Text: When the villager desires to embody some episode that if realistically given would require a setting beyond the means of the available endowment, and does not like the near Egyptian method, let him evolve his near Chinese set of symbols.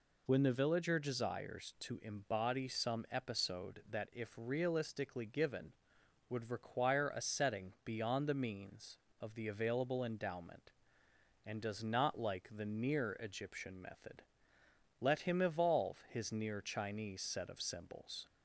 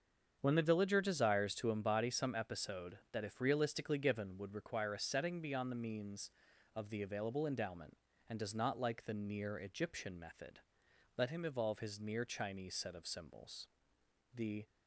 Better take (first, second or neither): first